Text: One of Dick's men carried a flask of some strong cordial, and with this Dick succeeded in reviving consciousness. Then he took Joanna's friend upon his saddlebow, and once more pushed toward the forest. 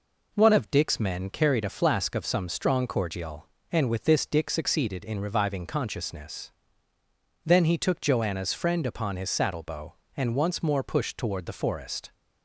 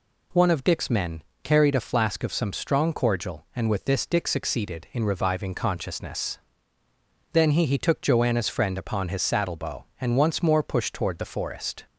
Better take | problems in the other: first | pauses between "men" and "carried"; slight; at 1.2 s; 0.20 s long // says "he" twice; at 7.6 s

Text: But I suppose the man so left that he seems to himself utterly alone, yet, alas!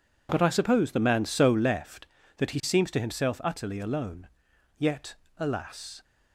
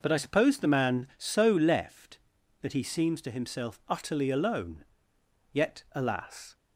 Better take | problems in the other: neither | none

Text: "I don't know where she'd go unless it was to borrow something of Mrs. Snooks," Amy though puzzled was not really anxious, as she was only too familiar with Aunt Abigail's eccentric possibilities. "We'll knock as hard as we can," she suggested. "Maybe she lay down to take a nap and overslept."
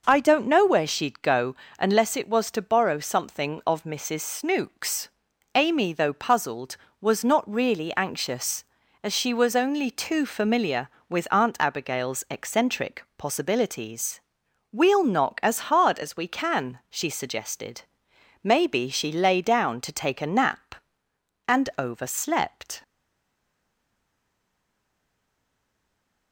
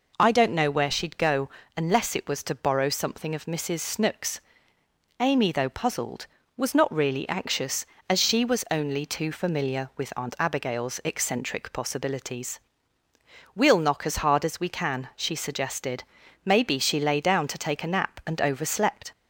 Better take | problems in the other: second | pauses between "go" and "unless"; slight; at 1.5 s; 0.24 s long; slight in the second // stays silent after the last word; strong; from 22.8 s on; 3.5 s long

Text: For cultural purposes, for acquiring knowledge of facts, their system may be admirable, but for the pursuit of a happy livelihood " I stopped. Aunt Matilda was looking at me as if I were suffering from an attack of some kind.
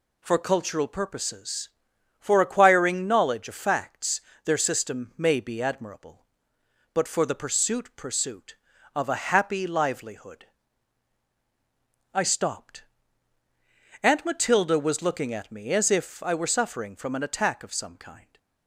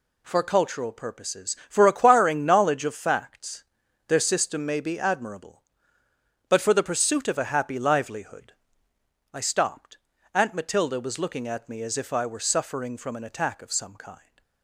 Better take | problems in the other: second | says "pursuit" twice; at 7.9 s

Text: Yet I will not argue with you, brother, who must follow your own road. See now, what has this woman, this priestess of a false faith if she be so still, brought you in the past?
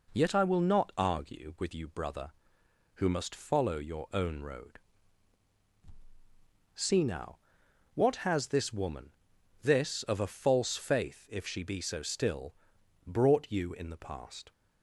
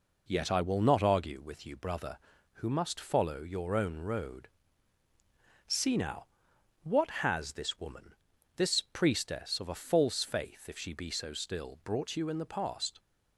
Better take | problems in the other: second | skips "priestess"; at 10.0 s

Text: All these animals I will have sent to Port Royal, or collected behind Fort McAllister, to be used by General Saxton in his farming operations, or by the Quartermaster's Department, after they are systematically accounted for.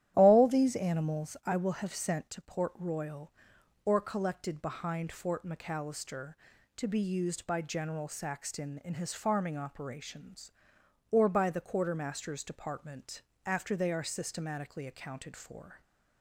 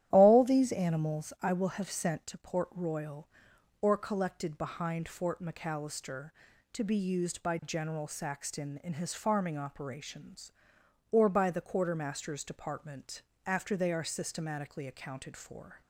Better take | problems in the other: neither | starts louder than the rest; strong; the same in both

